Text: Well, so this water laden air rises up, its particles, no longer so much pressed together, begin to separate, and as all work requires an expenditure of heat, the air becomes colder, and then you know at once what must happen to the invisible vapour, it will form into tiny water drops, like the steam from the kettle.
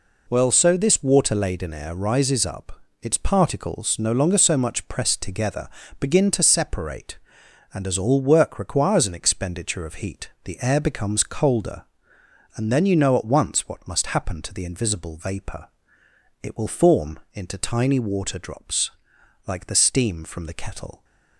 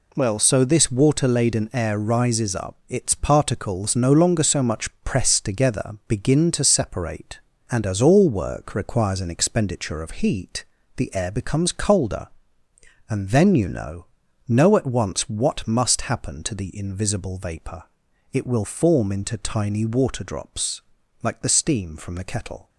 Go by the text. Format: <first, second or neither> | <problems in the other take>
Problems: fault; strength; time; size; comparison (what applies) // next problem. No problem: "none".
first | pauses between "much" and "pressed"; slight; at 4.8 s; 0.16 s long // says "know" twice; at 14.4 s